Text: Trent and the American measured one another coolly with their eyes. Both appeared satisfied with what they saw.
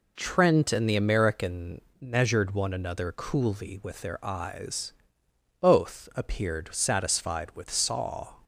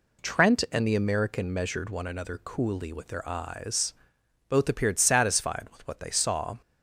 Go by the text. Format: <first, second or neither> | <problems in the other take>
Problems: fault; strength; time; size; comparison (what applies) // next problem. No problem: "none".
second | pauses between "American" and "measured"; slight; at 1.8 s; 0.18 s long // skips "what they"; at 7.7 s